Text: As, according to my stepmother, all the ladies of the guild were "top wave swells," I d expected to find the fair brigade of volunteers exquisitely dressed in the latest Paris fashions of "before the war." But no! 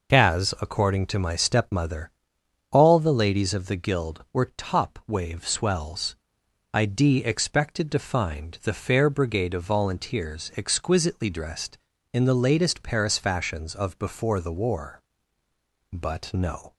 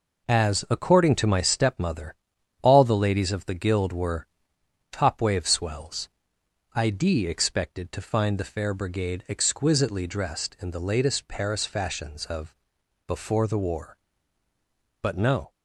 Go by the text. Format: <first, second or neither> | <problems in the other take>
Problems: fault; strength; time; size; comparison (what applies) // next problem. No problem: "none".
first | pauses between "were" and "top"; noticeable; at 4.2 s; 0.66 s long // skips "of volunteers"; at 9.2 s // pauses between "of" and "before"; noticeable; at 12.5 s; 0.52 s long